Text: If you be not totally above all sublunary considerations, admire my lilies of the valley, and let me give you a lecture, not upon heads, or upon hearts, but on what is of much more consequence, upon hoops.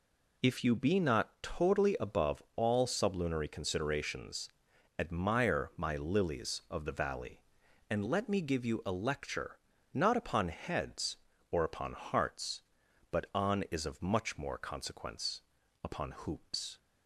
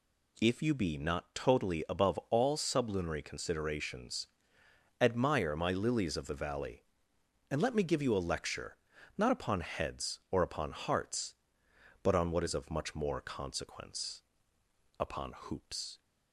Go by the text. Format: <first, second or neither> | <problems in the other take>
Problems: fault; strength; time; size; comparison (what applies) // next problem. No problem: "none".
second | skips "what"; at 13.6 s